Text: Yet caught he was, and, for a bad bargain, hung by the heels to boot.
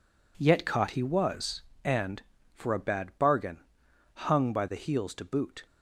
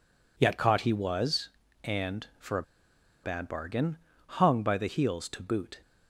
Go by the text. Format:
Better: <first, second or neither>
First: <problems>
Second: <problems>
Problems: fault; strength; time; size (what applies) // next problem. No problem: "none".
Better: first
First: none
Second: pauses between "a" and "bad"; noticeable; at 2.6 s; 0.61 s long